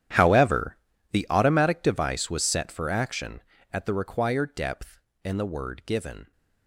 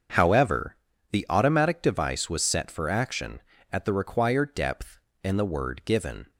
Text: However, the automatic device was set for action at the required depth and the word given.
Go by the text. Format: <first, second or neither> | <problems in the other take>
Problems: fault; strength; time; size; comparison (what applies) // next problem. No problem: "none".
second | gets quieter; strong; throughout; 19.5 dB // starts louder than the rest; strong; until 1.5 s; 10.5 dB; also in the second